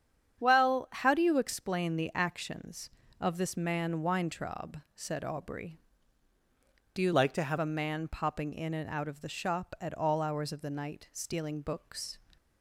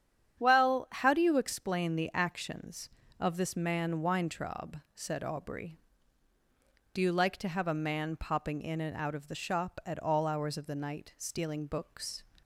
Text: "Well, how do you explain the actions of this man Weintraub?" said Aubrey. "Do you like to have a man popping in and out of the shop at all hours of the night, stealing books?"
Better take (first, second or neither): second